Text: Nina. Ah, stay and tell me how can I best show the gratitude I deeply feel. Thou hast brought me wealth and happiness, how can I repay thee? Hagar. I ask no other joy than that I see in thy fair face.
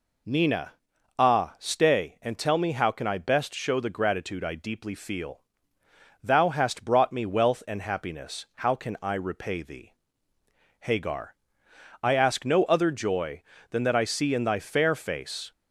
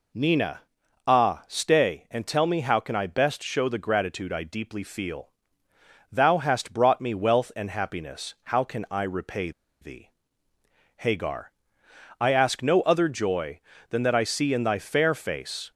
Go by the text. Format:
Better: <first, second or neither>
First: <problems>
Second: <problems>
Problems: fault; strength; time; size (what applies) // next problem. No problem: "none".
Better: first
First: none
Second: pauses between "repay" and "thee"; slight; at 9.5 s; 0.30 s long